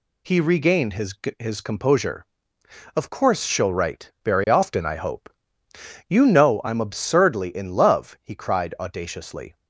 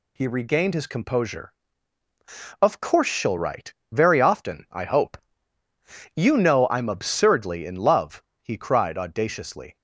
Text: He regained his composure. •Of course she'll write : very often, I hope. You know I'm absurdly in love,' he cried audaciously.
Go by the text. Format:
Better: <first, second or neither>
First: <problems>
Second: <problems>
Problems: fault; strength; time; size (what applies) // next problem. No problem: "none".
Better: second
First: says "his" twice; at 1.3 s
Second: none